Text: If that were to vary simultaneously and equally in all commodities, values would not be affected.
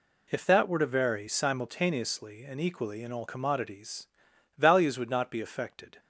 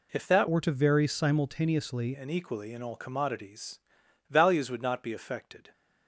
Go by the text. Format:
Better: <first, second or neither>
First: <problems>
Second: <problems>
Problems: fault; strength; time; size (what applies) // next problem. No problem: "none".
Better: first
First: none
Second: changes voice from "were" to "simultaneously"; from 0.5 to 2.1 s; 1.6 s long